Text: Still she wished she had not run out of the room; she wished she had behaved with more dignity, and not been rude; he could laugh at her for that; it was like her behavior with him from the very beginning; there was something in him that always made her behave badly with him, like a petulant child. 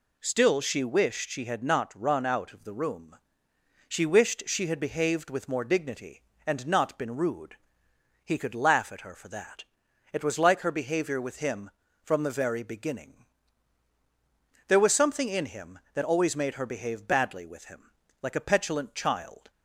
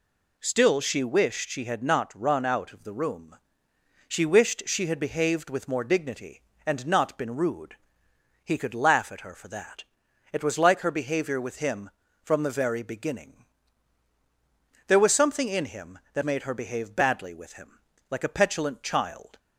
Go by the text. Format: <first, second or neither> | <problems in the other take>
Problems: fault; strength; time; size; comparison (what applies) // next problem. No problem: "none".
first | skips "always"; at 16.2 s